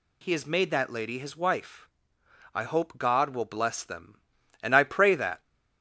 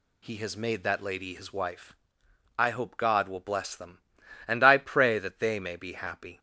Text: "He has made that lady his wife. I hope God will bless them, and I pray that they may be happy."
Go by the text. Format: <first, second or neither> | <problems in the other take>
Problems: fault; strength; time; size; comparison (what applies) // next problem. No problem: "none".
second | stops before "they may be happy"; at 5.4 s